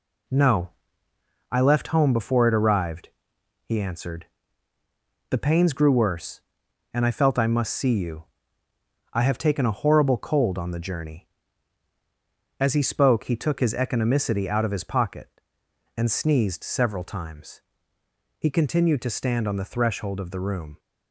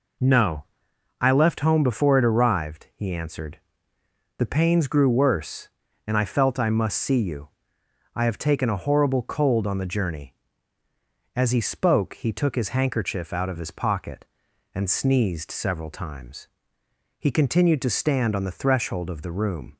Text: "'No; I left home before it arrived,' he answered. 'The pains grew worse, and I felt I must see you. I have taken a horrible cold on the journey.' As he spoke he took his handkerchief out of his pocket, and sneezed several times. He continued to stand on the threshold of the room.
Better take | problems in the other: second | says "economicity" for "handkerchief"; at 13.7 s

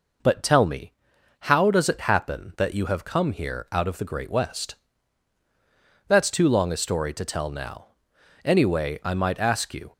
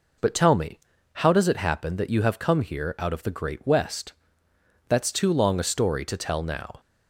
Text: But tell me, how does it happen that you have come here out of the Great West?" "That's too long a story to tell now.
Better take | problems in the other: second | goes on to say "Anyway I might ask you"; from 8.4 s on; 1.4 s long

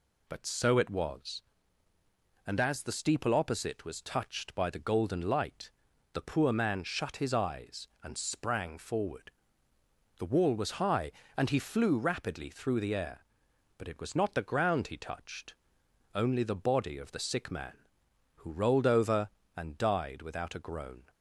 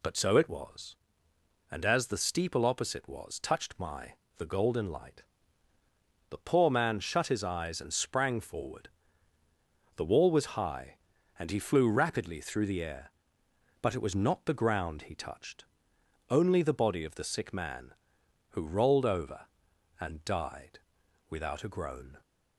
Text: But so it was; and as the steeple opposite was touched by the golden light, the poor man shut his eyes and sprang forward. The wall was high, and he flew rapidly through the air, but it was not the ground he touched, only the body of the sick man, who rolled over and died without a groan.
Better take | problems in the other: first | says "my" for "by"; at 3.7 s // pauses between "died" and "without"; noticeable; at 20.7 s; 0.50 s long

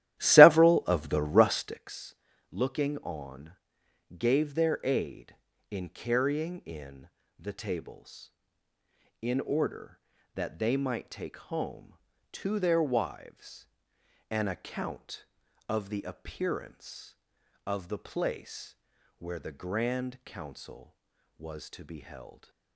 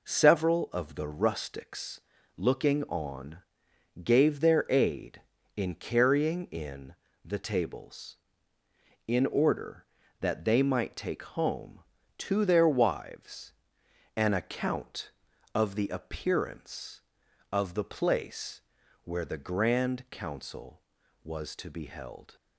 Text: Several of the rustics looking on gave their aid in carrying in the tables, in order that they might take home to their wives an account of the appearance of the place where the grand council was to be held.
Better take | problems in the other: second | starts louder than the rest; strong; until 1.9 s; 13.5 dB // pauses between "rustics" and "looking"; slight; at 2.1 s; 0.34 s long; slight in the second // pauses between "on" and "gave"; noticeable; at 3.5 s; 0.66 s long; noticeable in the second // pauses between "in" and "the"; slight; at 7.0 s; 0.30 s long; slight in the second // pauses between "wives" and "an"; noticeable; at 13.6 s; 0.60 s long; noticeable in the second // pauses between "place" and "where"; noticeable; at 18.7 s; 0.46 s long; noticeable in the second

